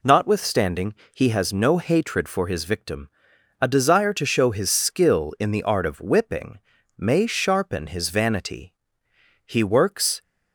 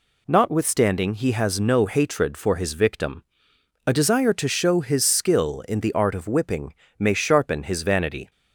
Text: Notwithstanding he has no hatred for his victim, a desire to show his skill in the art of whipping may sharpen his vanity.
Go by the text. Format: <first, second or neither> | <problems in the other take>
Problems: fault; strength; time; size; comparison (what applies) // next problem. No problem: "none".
second | pauses between "Notwithstanding" and "he"; slight; at 0.9 s; 0.18 s long // pauses between "whipping" and "may"; at 6.5 s; 0.38 s long; slight in the second // goes on to say "He works"; noticeable; from 9.4 s on; 0.76 s long